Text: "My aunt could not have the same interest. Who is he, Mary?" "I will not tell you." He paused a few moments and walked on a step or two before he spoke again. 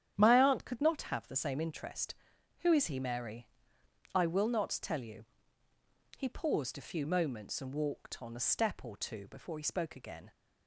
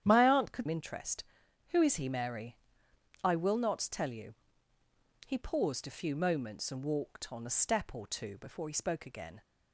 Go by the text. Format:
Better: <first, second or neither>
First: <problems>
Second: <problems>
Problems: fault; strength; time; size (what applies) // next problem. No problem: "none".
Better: first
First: starts louder than the rest; strong; until 1.1 s; 10 dB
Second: starts louder than the rest; strong; until 1.0 s; 10 dB // skips "not have the same"; at 0.6 s